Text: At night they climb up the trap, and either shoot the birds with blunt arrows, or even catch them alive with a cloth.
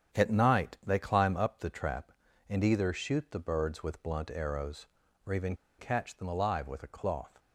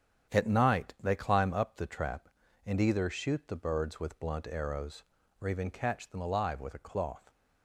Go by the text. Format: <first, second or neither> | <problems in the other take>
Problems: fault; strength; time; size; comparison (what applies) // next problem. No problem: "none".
second | starts louder than the rest; strong; until 1.2 s; 8.5 dB; strong in the second // pauses between "even" and "catch"; slight; at 5.5 s; 0.23 s long